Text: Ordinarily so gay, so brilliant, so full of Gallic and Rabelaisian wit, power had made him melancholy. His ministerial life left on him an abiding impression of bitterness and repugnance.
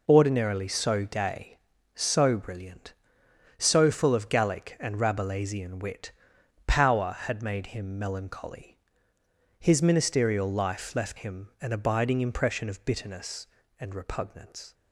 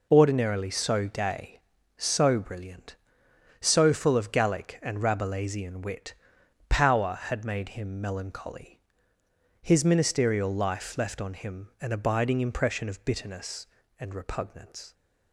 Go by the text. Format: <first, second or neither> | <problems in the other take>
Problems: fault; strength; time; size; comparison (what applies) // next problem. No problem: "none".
second | skips "on"; at 11.1 s